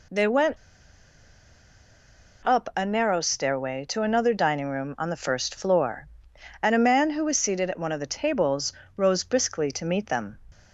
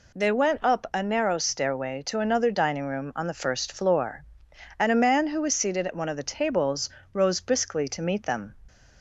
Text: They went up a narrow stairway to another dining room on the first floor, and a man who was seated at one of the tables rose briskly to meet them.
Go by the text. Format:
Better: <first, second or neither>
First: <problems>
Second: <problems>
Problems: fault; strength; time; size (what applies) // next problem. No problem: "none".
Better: second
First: pauses between "went" and "up"; strong; at 0.5 s; 1.8 s long // pauses between "tables" and "rose"; slight; at 8.7 s; 0.24 s long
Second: pauses between "tables" and "rose"; slight; at 6.8 s; 0.24 s long